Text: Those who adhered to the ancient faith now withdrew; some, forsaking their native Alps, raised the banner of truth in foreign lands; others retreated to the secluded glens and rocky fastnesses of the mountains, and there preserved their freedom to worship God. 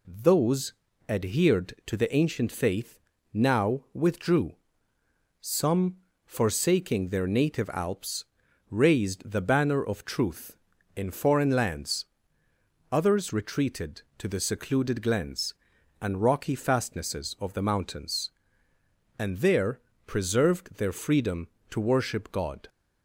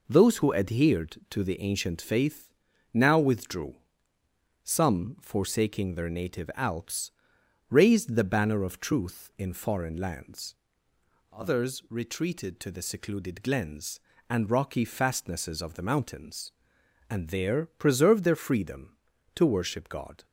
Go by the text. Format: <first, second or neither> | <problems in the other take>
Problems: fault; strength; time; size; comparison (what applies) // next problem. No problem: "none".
second | skips "who"; at 0.8 s // pauses between "faith" and "now"; slight; at 2.9 s; 0.34 s long; also in the second // pauses between "there" and "preserved"; slight; at 19.8 s; 0.24 s long